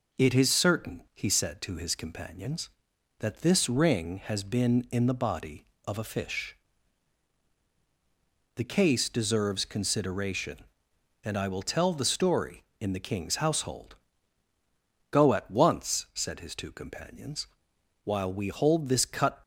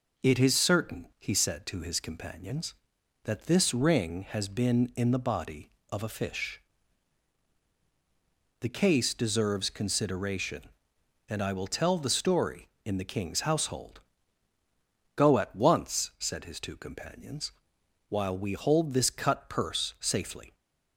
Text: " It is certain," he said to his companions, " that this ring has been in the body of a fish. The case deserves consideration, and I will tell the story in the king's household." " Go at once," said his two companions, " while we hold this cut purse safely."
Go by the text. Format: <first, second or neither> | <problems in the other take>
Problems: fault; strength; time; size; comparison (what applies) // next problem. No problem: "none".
second | stops before "purse safely"; at 19.4 s